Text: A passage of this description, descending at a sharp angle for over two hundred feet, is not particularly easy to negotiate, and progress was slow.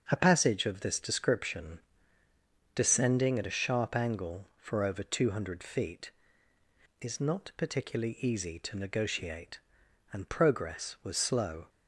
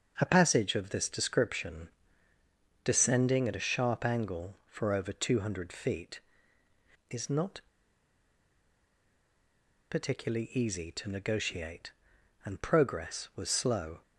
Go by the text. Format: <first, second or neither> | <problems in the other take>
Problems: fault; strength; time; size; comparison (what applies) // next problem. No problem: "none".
first | starts louder than the rest; until 1.1 s; 6.5 dB; also in the first // pauses between "not" and "particularly"; strong; at 7.6 s; 2.3 s long